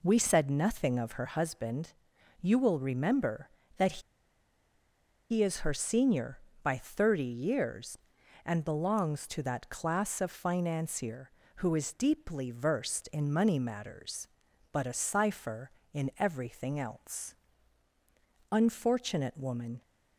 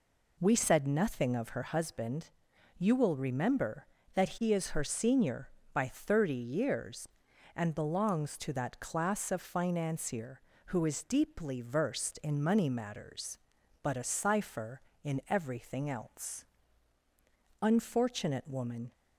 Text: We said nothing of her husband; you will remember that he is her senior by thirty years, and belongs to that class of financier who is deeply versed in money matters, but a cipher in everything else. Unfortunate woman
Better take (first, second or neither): second